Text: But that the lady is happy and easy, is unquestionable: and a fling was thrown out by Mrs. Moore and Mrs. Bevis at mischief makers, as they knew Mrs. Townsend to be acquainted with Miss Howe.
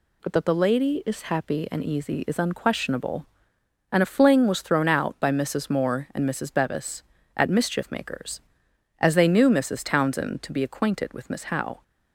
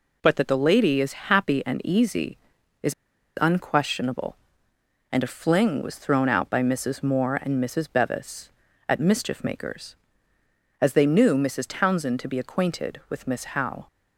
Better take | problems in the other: first | pauses between "is" and "unquestionable"; noticeable; at 2.9 s; 0.46 s long

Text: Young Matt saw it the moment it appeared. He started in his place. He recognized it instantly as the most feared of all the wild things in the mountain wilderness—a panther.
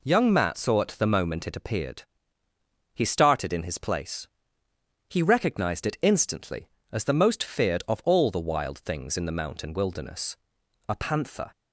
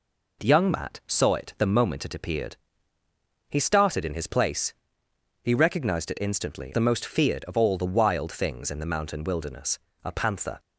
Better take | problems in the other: first | skips "as"; at 6.7 s

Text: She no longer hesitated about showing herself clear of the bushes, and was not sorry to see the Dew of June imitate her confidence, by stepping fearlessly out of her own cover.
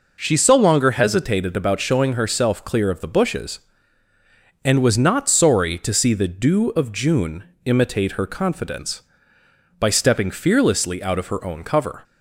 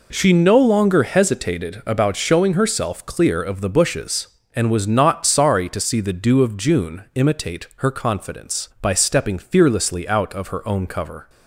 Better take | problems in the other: second | says "so" for "no"; at 0.3 s // pauses between "June" and "imitate"; slight; at 7.4 s; 0.18 s long

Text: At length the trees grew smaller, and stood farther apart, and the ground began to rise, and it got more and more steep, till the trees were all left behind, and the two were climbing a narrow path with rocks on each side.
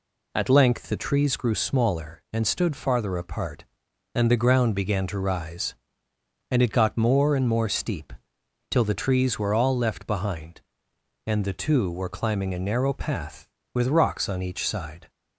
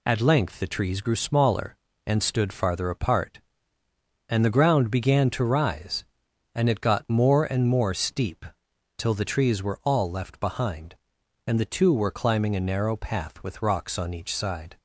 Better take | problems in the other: neither | none

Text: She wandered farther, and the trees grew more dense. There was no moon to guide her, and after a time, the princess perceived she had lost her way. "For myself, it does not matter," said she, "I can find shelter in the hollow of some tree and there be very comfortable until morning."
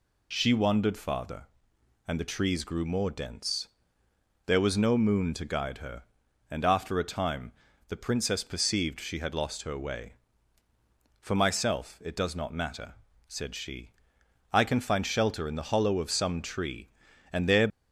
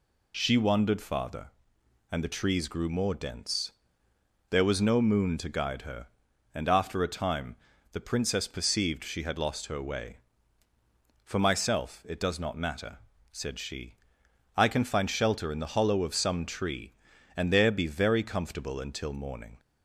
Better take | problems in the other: second | stops before "be very comfortable until morning"; at 17.6 s

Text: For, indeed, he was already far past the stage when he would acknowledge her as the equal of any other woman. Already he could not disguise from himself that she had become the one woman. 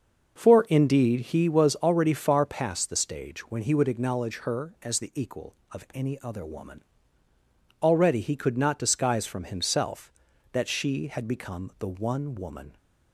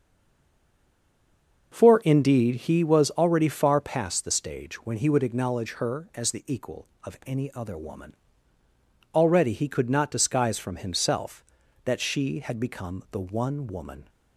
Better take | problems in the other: first | stays silent before the first word; noticeable; until 1.7 s; 1.7 s long // starts louder than the rest; noticeable; until 2.7 s; 6 dB; noticeable in the first

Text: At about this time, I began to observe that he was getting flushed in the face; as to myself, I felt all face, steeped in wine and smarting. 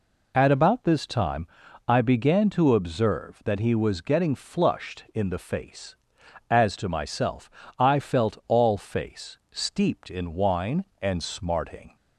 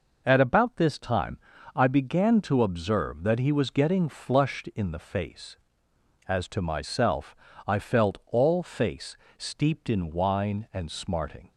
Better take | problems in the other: neither | none

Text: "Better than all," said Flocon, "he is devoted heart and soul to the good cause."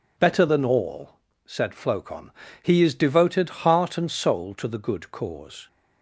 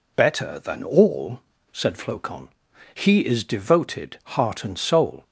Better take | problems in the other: first | stops before "to the good cause"; at 5.2 s

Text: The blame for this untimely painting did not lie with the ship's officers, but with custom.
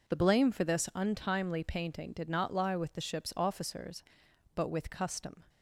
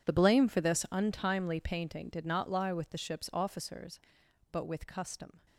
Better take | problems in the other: first | gets quieter; strong; throughout; 18 dB

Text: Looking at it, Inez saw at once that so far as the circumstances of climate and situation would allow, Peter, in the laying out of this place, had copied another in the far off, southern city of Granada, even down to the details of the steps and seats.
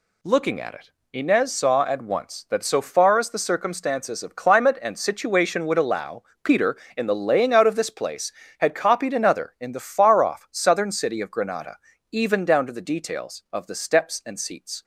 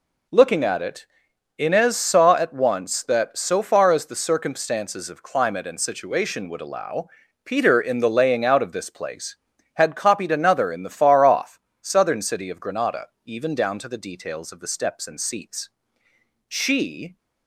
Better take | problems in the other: first | goes on to say "She"; noticeable; from 16.4 s on; 0.70 s long

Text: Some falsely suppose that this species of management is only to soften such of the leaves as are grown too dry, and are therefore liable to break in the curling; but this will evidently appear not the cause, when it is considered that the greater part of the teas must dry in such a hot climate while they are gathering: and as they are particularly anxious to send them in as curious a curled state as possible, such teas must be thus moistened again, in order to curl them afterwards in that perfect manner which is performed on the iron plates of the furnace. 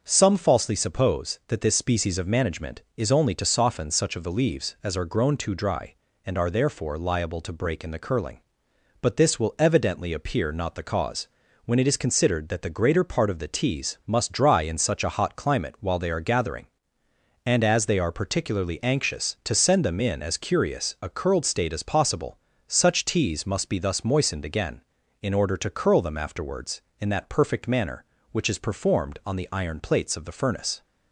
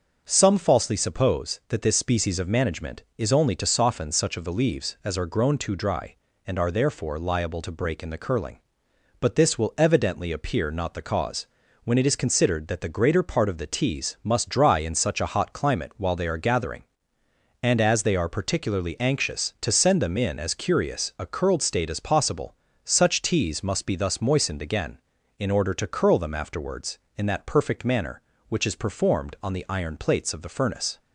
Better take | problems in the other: neither | starts louder than the rest; noticeable; the same in both

